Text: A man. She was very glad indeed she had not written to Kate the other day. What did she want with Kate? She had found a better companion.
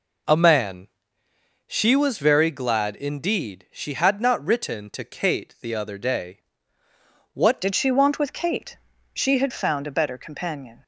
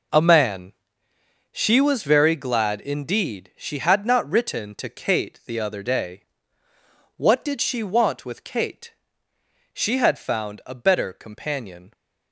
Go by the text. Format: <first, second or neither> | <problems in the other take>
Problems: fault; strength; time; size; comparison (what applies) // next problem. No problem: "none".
second | changes voice at "did"; from 7.6 s on; 3.2 s long